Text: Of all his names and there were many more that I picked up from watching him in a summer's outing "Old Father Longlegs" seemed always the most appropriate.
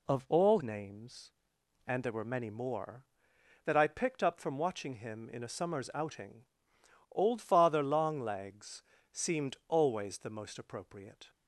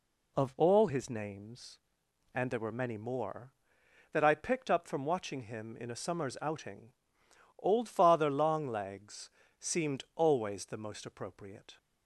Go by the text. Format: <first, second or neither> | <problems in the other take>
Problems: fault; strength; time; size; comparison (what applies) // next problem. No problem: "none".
second | skips "his"; at 0.6 s // pauses between "outing" and "Old"; noticeable; at 6.4 s; 0.70 s long; noticeable in the second // pauses between "Longlegs" and "seemed"; slight; at 8.8 s; 0.30 s long; slight in the second